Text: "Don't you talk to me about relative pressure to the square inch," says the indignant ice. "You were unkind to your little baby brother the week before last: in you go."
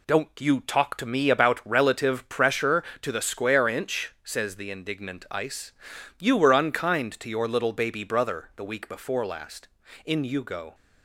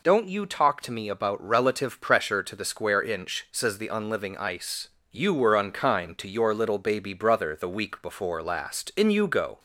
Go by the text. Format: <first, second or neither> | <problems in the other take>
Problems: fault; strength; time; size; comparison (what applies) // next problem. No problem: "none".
first | says "unliving" for "indignant"; at 3.8 s